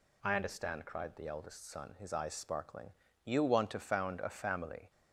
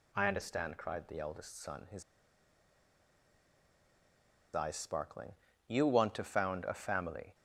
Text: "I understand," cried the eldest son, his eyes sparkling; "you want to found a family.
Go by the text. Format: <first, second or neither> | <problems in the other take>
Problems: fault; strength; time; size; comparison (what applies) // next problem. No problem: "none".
first | pauses between "his" and "eyes"; strong; at 2.0 s; 2.5 s long